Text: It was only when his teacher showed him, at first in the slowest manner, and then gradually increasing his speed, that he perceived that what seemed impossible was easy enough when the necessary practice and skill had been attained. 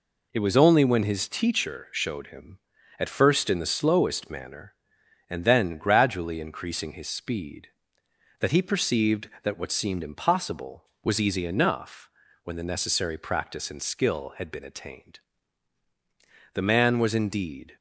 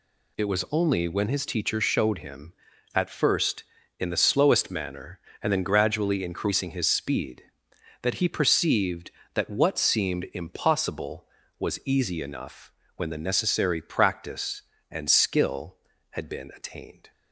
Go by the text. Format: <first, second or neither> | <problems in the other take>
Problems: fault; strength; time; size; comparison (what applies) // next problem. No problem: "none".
second | pauses between "enough" and "when"; slight; at 12.0 s; 0.34 s long; slight in the second // goes on to say "The man was indeed"; noticeable; from 16.5 s on; 1.2 s long